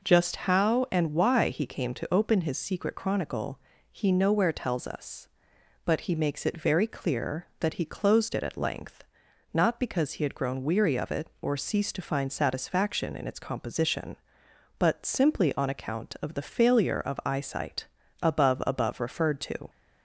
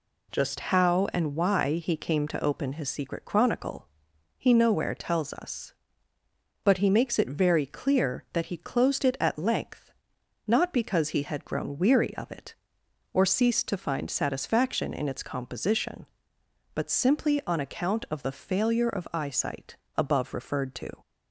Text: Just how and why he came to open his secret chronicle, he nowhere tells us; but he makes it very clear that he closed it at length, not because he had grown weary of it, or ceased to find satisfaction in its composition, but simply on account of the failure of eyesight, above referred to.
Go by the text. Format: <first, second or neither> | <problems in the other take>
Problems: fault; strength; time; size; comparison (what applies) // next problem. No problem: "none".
second | says "above" twice; at 18.6 s